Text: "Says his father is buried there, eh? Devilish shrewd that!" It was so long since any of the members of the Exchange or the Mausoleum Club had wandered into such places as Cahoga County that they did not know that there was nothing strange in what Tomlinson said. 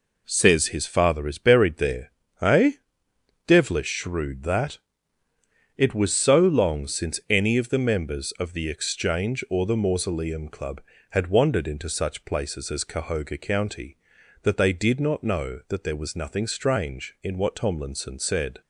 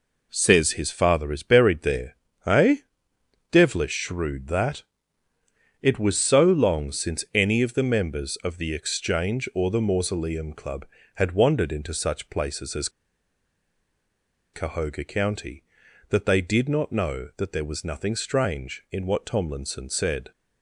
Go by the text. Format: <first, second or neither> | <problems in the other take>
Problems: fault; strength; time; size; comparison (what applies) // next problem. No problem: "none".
first | pauses between "as" and "Cahoga"; strong; at 12.8 s; 1.6 s long